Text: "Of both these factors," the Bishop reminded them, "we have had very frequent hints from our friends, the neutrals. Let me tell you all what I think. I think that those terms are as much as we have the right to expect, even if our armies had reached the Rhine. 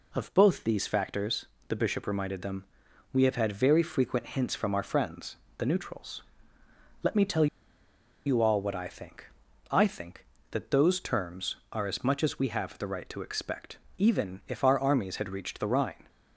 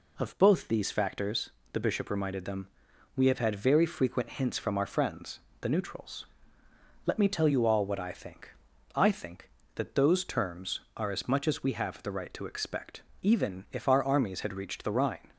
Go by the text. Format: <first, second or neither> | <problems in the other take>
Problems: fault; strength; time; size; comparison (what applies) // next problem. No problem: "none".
second | pauses between "tell" and "you"; noticeable; at 7.4 s; 0.79 s long